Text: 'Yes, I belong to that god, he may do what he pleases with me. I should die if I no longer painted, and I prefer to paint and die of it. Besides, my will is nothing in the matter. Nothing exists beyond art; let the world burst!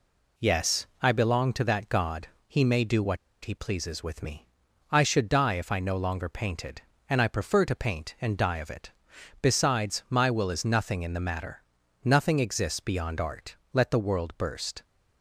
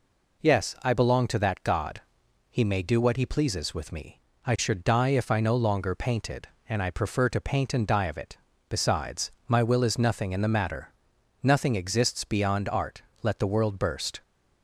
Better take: second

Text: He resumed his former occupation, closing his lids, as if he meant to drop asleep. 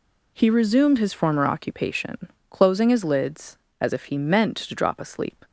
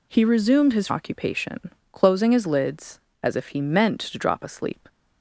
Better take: first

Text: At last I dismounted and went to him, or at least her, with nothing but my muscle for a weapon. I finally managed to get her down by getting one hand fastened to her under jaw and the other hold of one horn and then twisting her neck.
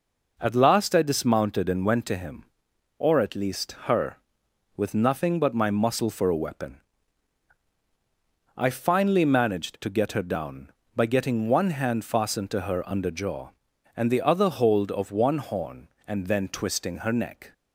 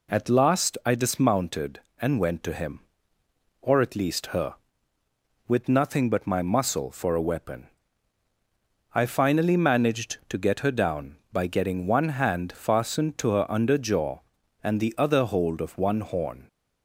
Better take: first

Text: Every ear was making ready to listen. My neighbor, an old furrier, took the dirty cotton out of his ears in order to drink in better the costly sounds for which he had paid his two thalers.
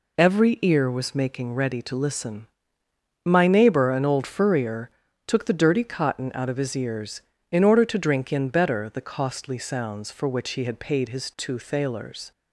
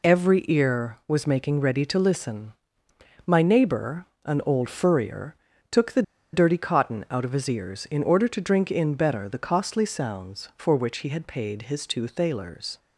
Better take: first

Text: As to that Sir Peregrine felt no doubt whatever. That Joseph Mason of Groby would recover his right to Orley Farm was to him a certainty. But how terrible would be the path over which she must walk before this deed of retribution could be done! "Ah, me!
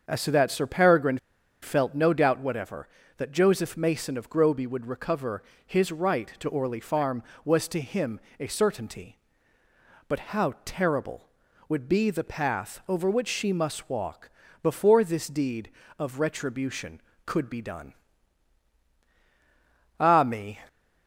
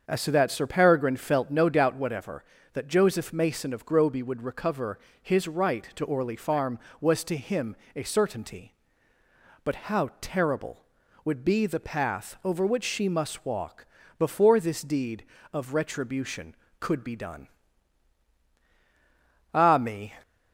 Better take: second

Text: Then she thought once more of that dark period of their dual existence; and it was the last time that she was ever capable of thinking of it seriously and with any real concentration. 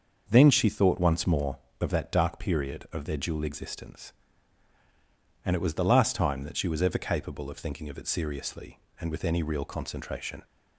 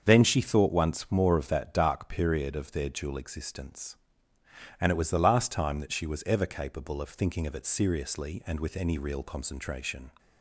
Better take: neither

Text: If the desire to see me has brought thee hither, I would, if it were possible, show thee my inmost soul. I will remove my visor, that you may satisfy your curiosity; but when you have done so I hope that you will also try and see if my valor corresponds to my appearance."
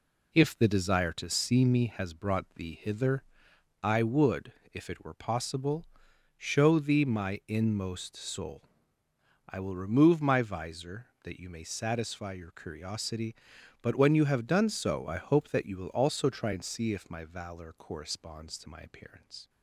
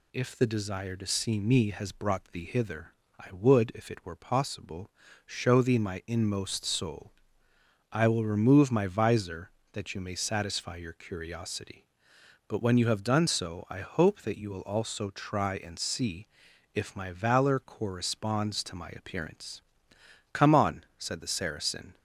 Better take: first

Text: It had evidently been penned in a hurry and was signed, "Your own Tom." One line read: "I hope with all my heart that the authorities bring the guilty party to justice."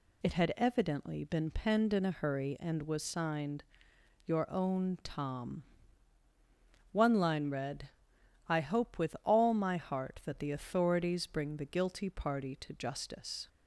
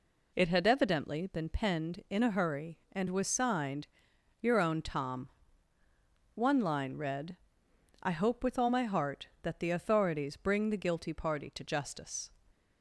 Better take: neither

